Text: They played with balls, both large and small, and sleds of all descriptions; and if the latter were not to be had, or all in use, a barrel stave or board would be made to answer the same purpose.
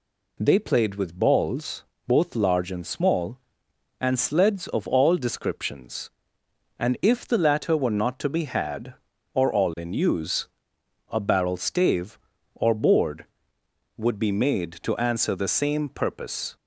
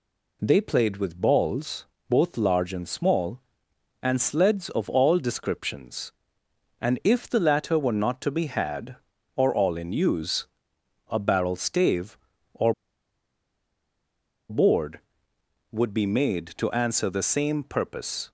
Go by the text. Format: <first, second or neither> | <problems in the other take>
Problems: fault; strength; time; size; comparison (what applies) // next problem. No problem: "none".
first | pauses between "or" and "board"; strong; at 12.7 s; 1.7 s long